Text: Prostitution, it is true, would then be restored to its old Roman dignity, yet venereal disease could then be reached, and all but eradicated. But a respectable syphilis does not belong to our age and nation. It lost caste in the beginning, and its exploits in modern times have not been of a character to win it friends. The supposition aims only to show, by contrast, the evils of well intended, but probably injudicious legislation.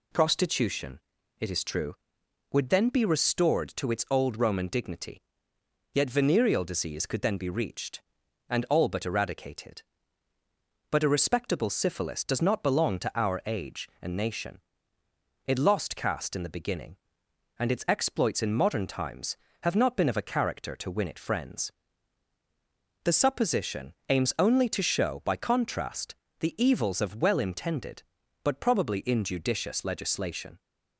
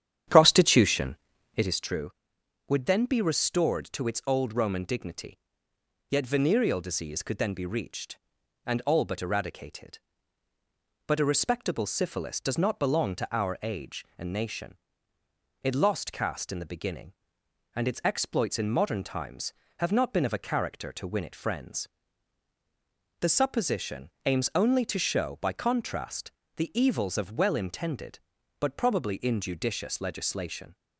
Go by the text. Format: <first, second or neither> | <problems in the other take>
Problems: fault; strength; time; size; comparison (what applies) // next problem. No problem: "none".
first | starts louder than the rest; strong; until 1.8 s; 10 dB // pauses between "supposition" and "aims"; slight; at 24.1 s; 0.16 s long; slight in the first